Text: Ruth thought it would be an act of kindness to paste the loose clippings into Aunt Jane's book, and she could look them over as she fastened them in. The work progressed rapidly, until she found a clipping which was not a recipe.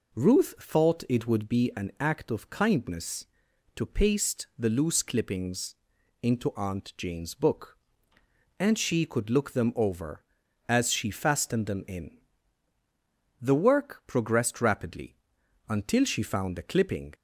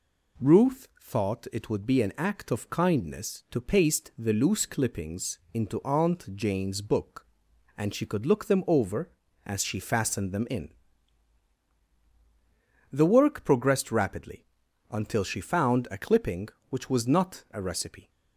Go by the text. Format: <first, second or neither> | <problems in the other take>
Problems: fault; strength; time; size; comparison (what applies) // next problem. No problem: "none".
second | pauses between "clippings" and "into"; noticeable; at 5.7 s; 0.46 s long; slight in the second // stops before "which was not a recipe"; at 17.1 s